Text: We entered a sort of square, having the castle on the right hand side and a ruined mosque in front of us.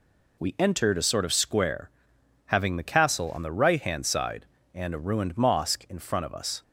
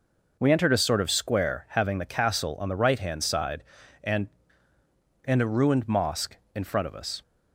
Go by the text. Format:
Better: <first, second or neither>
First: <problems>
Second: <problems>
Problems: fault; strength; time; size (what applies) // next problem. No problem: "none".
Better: first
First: none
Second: says "and" twice; at 5.2 s